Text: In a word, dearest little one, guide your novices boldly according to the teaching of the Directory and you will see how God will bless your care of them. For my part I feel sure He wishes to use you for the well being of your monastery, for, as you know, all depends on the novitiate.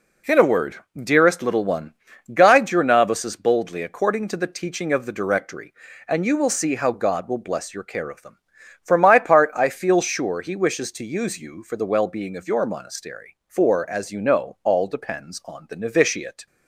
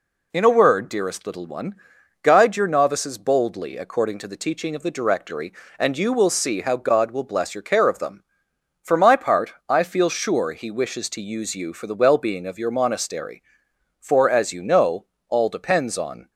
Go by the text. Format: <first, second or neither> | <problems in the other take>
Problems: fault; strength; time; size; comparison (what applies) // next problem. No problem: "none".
first | stops before "the novitiate"; at 16.3 s